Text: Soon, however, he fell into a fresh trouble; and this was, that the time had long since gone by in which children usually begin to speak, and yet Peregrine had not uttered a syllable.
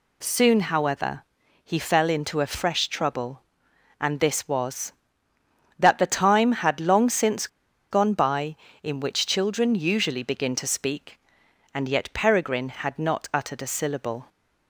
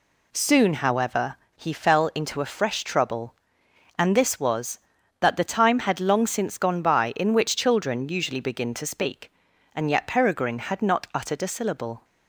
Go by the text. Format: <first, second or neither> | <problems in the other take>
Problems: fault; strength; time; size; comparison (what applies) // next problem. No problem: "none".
second | pauses between "since" and "gone"; at 7.4 s; 0.43 s long